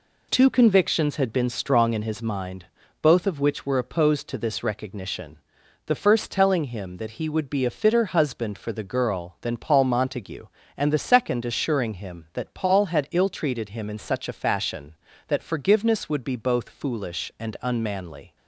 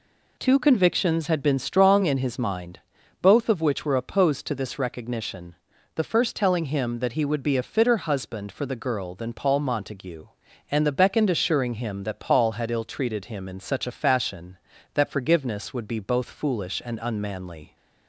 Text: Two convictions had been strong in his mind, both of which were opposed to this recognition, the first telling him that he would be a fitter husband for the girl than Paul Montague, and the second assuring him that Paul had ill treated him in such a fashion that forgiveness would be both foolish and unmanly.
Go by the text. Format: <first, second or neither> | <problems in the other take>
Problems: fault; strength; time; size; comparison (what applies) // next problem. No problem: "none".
first | says "beckoned" for "second"; at 10.9 s